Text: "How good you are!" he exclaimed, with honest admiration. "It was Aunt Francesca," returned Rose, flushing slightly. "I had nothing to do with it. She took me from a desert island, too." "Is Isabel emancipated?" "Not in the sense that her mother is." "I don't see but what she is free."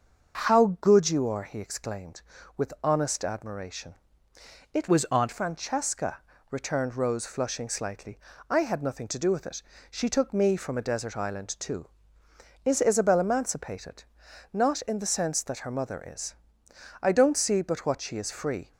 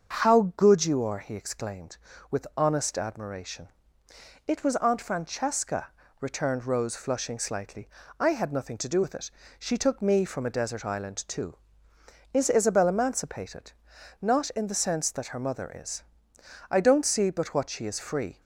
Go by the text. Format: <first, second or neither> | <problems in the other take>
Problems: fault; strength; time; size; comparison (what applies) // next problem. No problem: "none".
second | starts louder than the rest; noticeable; until 1.5 s; 6 dB; also in the second // changes voice from "was" to "Aunt"; from 4.8 to 5.2 s; 0.4 s long